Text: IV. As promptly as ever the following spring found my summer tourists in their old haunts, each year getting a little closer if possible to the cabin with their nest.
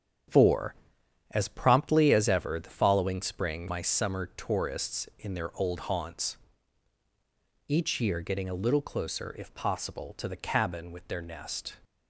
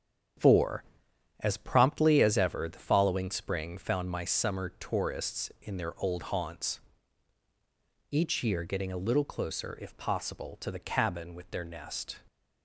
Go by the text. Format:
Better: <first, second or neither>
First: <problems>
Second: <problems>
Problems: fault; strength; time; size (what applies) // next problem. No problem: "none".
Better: second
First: starts louder than the rest; strong; until 1.8 s; 8.5 dB // skips "found"; at 3.6 s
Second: starts louder than the rest; strong; until 1.9 s; 8.5 dB